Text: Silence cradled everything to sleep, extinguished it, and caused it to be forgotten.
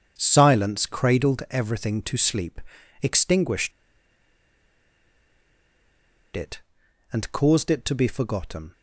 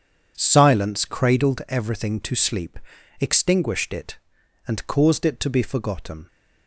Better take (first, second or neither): second